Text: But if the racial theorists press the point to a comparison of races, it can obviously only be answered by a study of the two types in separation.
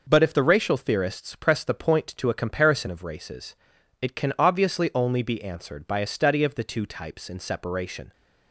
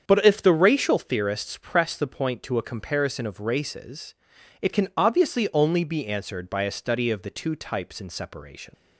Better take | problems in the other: first | starts louder than the rest; strong; until 1.0 s; 7.5 dB // leaves "separation" unfinished; at 8.7 s; 95 ms

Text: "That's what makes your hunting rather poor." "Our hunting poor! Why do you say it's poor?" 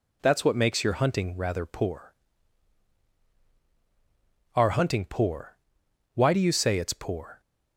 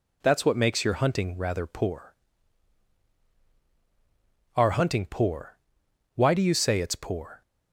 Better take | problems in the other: neither | none

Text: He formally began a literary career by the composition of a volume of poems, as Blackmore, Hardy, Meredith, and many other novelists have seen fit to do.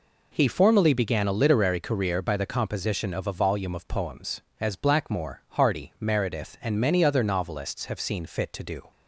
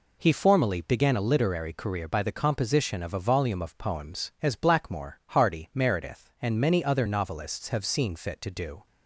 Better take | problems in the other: neither | none

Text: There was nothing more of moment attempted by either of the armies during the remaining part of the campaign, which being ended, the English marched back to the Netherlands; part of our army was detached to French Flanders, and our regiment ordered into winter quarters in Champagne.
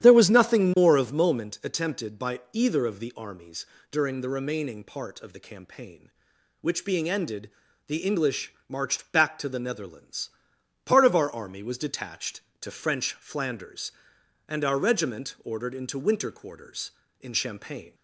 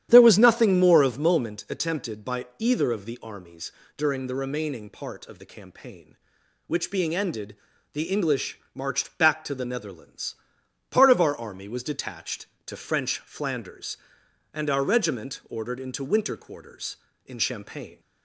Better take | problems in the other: neither | starts louder than the rest; strong; the same in both // pauses between "armies" and "during"; slight; the same in both // pauses between "English" and "marched"; slight; the same in both

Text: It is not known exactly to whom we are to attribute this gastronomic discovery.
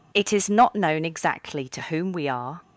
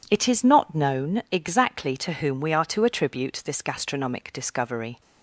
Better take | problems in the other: second | stops before "to attribute this gastronomic discovery"; at 2.6 s

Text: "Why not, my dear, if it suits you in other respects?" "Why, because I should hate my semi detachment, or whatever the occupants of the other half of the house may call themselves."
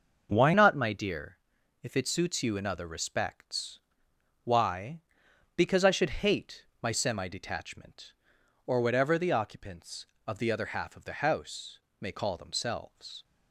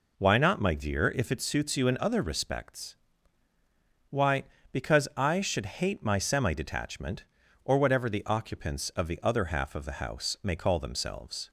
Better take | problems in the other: second | starts louder than the rest; noticeable; until 1.3 s; 6 dB // changes voice at "not"; from 0.5 s on; 12.7 s long // pauses between "hate" and "my"; slight; at 6.6 s; 0.16 s long // pauses between "house" and "may"; slight; at 11.7 s; 0.22 s long

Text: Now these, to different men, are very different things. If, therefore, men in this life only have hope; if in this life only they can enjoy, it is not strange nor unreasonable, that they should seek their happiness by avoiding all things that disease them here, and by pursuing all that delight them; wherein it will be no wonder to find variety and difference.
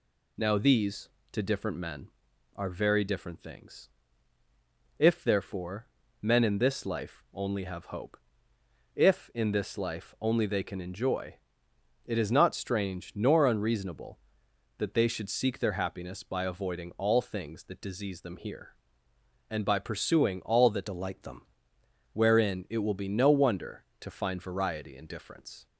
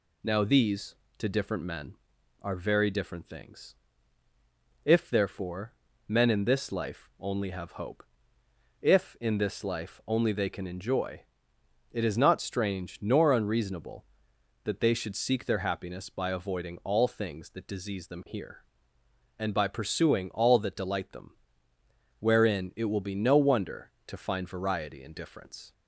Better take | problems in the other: second | changes voice from "delight" to "them"; from 20.8 to 21.4 s; 0.6 s long

